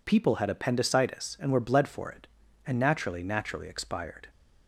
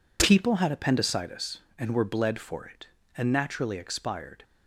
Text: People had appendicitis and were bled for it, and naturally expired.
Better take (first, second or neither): second